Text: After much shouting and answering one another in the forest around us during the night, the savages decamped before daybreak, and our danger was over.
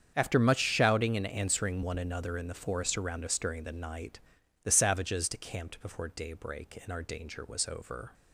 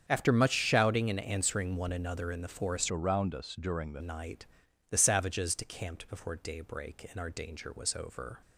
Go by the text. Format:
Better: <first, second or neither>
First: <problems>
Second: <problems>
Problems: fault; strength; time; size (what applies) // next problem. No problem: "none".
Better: first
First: starts louder than the rest; strong; until 1.1 s; 7.5 dB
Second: starts louder than the rest; strong; until 1.0 s; 8 dB // changes voice from "around" to "the"; from 2.9 to 4.0 s; 1.1 s long